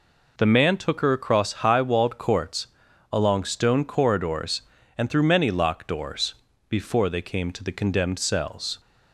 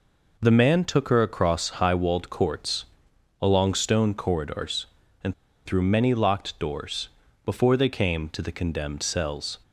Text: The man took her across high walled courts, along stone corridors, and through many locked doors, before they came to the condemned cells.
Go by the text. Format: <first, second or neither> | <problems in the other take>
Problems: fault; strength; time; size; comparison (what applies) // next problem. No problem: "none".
first | pauses between "and" and "through"; slight; at 5.3 s; 0.32 s long